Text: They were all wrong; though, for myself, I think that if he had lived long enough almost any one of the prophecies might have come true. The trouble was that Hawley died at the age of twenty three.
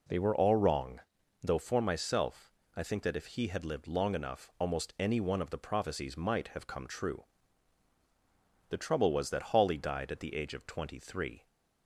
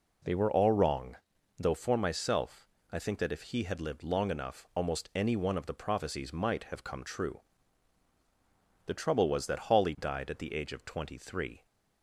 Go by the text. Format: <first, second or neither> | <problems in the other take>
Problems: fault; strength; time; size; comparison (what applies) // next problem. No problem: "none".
neither | none